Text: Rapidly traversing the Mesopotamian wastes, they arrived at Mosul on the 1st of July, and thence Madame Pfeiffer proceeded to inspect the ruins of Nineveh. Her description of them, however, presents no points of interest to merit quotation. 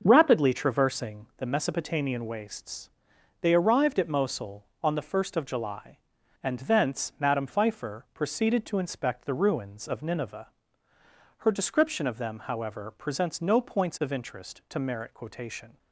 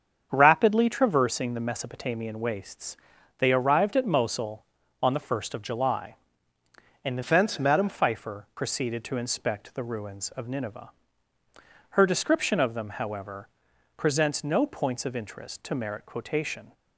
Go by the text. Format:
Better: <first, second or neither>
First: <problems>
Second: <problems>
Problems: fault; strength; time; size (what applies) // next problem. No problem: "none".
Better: first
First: starts louder than the rest; until 1.0 s; 6.5 dB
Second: starts louder than the rest; strong; until 1.3 s; 7.5 dB // changes voice from "thence" to "Madame"; from 7.2 to 7.8 s; 0.6 s long